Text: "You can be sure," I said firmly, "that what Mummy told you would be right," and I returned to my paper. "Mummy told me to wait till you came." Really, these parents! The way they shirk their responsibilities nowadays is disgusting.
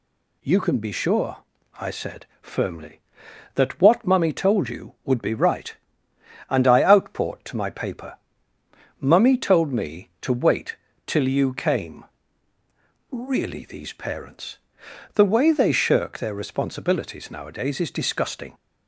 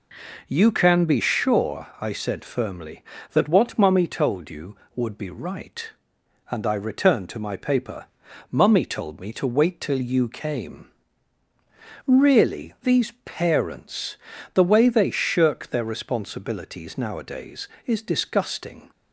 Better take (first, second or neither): second